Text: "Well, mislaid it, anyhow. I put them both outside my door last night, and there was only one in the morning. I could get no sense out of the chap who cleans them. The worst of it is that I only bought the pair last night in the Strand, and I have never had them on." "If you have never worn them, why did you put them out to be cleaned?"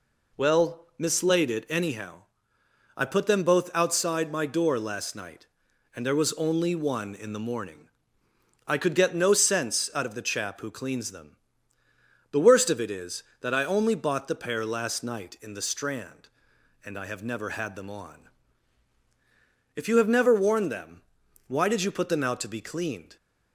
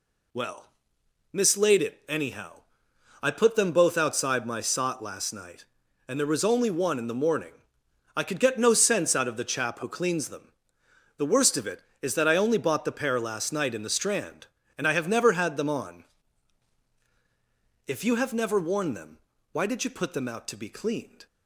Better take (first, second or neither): first